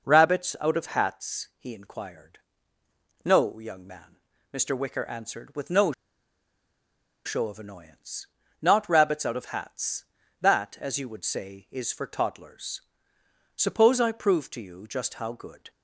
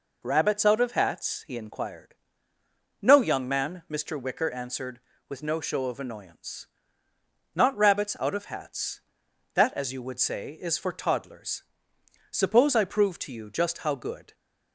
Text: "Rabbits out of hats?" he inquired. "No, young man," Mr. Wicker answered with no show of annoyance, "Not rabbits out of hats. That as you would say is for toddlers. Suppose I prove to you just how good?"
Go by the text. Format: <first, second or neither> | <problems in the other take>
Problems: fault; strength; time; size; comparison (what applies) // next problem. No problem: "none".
second | pauses between "no" and "show"; strong; at 5.9 s; 1.3 s long